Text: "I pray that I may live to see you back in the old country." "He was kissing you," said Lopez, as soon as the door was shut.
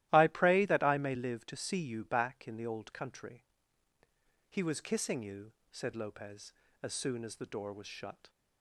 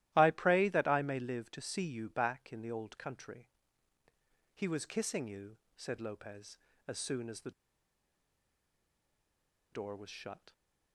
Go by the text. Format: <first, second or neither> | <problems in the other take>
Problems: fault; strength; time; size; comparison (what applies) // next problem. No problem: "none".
first | starts louder than the rest; strong; until 1.1 s; 15 dB; strong in the first // pauses between "the" and "door"; strong; at 7.5 s; 2.2 s long